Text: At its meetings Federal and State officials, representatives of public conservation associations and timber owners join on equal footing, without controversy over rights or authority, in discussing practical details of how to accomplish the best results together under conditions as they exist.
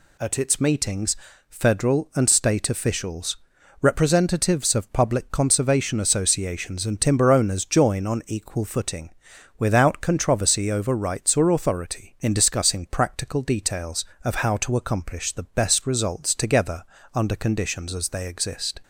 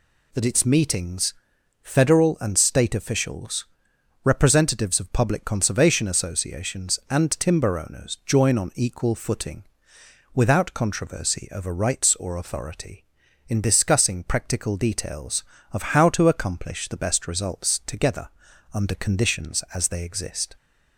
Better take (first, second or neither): first